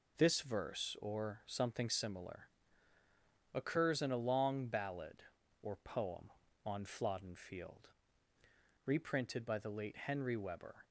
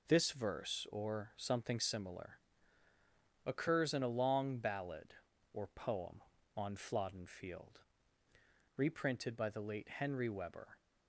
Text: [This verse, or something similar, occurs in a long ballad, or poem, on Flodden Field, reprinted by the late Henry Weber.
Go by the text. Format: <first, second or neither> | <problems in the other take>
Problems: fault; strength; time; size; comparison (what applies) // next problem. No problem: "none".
neither | none